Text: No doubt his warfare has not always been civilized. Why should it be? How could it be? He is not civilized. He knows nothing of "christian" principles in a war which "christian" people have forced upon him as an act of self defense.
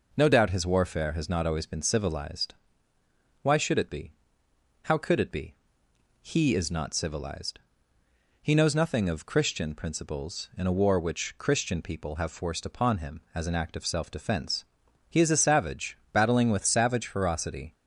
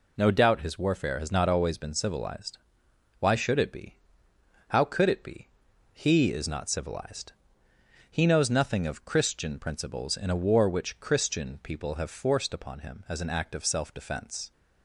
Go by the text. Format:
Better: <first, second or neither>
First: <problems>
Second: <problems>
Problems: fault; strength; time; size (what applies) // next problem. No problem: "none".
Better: second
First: goes on to say "He is a savage battling with savage ferocity"; strong; from 15.0 s on; 2.6 s long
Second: none